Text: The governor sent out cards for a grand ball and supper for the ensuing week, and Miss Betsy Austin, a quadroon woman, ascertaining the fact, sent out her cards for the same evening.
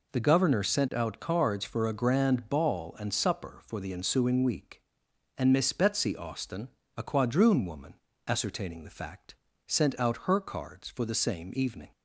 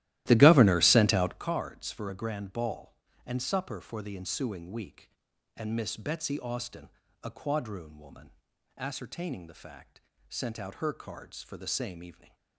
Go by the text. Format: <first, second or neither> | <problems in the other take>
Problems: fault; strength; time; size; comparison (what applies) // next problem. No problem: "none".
first | starts louder than the rest; strong; until 1.4 s; 15.5 dB